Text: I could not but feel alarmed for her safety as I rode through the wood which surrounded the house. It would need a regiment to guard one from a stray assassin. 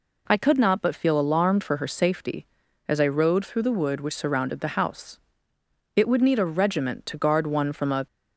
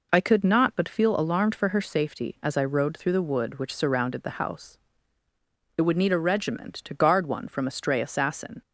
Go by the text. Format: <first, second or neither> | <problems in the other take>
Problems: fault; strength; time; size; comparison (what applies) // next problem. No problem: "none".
second | stops before "stray assassin"; at 8.0 s